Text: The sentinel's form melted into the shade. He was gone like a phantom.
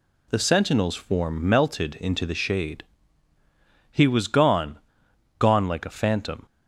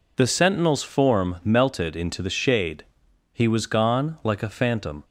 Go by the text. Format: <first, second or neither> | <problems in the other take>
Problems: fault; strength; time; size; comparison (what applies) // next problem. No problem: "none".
second | says "gone" twice; at 5.3 s